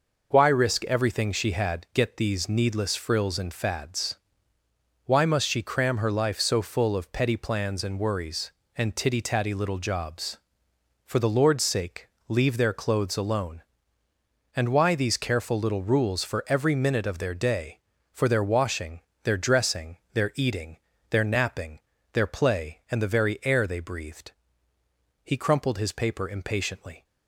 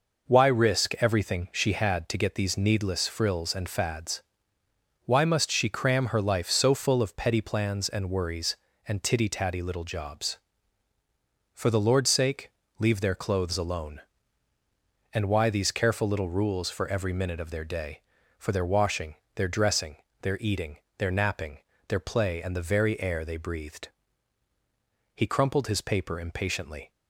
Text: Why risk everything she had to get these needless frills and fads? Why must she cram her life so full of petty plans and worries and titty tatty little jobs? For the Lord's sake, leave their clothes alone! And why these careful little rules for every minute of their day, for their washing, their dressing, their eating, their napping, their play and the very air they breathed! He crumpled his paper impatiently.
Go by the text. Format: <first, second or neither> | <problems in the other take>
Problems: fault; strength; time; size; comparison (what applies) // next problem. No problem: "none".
second | skips "to"; at 1.8 s